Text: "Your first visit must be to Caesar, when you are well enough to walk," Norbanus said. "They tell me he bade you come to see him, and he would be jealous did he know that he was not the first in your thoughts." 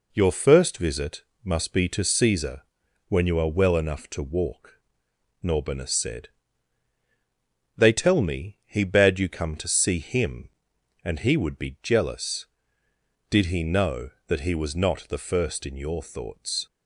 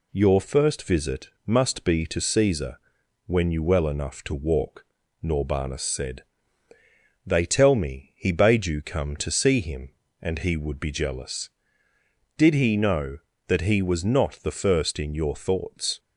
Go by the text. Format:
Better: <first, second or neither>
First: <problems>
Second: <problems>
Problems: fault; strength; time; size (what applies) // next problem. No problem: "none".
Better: first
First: pauses between "visit" and "must"; slight; at 1.2 s; 0.22 s long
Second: pauses between "visit" and "must"; slight; at 1.2 s; 0.16 s long // skips "are"; at 3.6 s